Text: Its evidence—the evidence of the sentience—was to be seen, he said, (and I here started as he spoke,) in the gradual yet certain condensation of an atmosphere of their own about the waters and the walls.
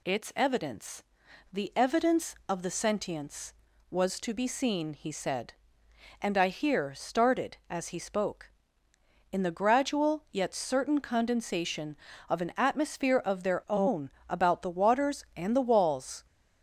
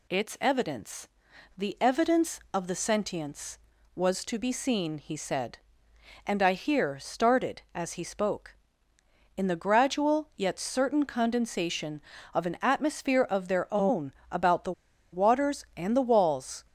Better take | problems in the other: first | pauses between "own" and "about"; slight; at 14.1 s; 0.18 s long; slight in the first // pauses between "the" and "waters"; at 14.7 s; 0.40 s long

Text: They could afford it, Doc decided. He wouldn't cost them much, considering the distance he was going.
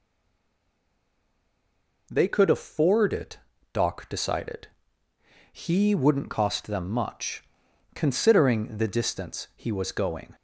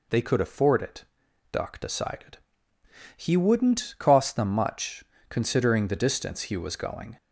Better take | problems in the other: second | stays silent before the first word; noticeable; until 2.0 s; 2.0 s long

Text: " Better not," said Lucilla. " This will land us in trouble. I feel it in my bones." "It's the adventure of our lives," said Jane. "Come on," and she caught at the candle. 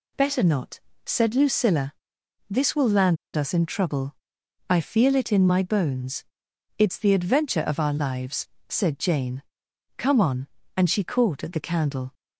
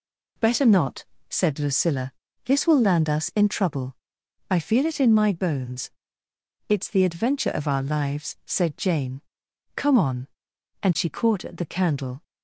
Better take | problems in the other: second | pauses between "land" and "us"; slight; at 3.1 s; 0.18 s long

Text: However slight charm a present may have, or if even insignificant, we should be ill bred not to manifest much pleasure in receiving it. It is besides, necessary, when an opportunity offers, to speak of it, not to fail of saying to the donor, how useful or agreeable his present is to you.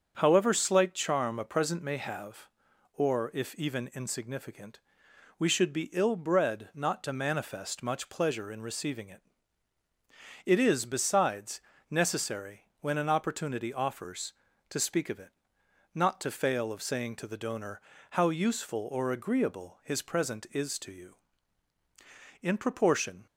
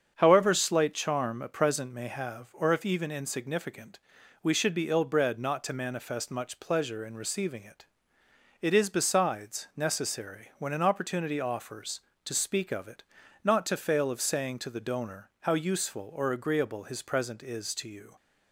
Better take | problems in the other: second | starts louder than the rest; until 1.1 s; 6.5 dB; strong in the second // goes on to say "In proportion"; noticeable; from 22.4 s on; 0.84 s long

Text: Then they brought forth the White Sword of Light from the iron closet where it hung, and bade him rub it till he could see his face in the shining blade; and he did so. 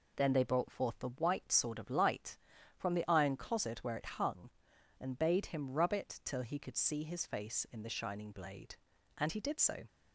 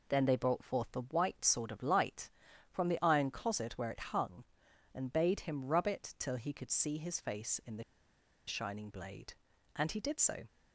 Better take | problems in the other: first | pauses between "the" and "shining"; noticeable; at 7.8 s; 0.64 s long

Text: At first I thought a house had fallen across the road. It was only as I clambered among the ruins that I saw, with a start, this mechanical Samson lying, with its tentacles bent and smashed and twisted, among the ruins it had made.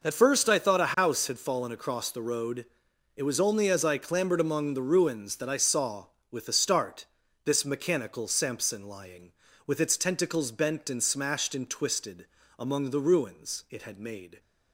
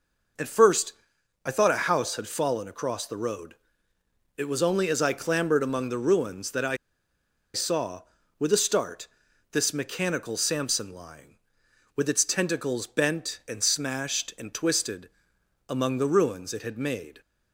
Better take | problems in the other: first | pauses between "first" and "I"; noticeable; at 0.9 s; 0.52 s long // pauses between "I" and "saw"; noticeable; at 6.7 s; 0.78 s long

